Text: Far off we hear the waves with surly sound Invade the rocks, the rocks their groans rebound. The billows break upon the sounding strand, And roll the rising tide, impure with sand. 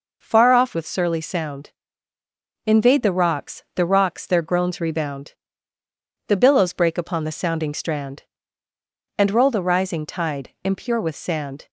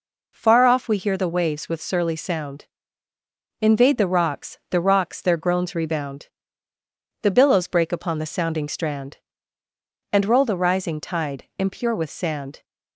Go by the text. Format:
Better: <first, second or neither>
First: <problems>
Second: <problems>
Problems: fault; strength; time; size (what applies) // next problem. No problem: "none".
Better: second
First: skips "we hear the waves"; at 0.7 s // pauses between "sound" and "Invade"; noticeable; at 1.7 s; 0.96 s long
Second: pauses between "sound" and "Invade"; noticeable; at 2.6 s; 0.96 s long